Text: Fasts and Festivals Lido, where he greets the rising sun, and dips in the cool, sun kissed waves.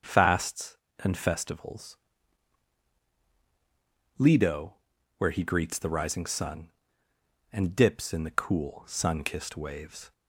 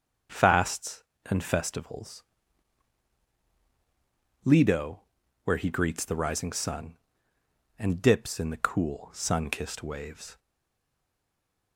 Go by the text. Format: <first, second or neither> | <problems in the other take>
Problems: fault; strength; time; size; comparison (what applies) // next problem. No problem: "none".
first | starts louder than the rest; until 1.5 s; 6.5 dB; also in the first // pauses between "Festivals" and "Lido"; strong; at 2.2 s; 2.2 s long; strong in the first // stays silent after the last word; noticeable; from 10.3 s on; 1.4 s long